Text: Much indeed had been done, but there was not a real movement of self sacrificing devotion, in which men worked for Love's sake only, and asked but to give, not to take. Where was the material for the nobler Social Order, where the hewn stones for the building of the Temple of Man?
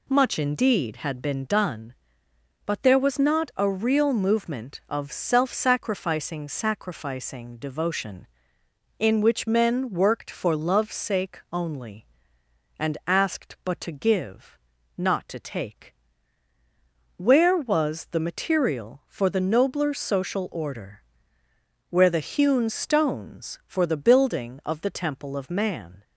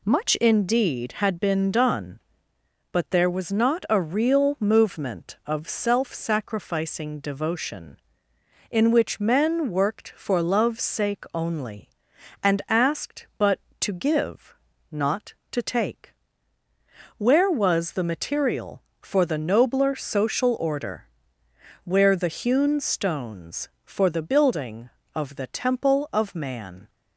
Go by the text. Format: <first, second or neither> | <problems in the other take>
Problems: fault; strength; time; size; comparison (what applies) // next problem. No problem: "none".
second | says "sacrificing" twice; at 6.4 s